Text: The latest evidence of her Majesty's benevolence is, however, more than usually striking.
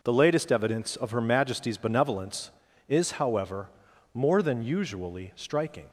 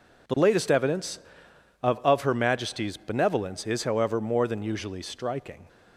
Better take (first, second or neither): first